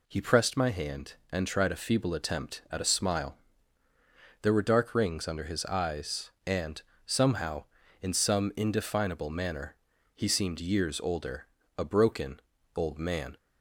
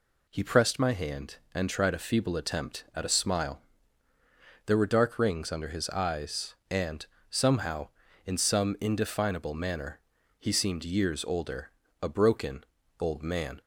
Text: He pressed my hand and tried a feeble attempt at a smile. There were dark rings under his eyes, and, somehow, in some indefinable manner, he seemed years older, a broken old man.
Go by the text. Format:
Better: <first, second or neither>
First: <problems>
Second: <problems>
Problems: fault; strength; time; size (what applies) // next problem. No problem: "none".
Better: neither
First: pauses between "broken" and "old"; slight; at 12.4 s; 0.34 s long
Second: pauses between "broken" and "old"; slight; at 12.6 s; 0.34 s long